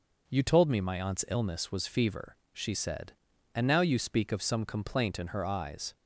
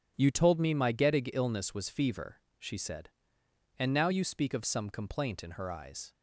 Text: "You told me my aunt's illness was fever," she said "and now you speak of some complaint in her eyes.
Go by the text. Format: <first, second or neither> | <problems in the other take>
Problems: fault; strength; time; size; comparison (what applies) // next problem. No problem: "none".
first | says "gettig" for "aunt's"; at 0.9 s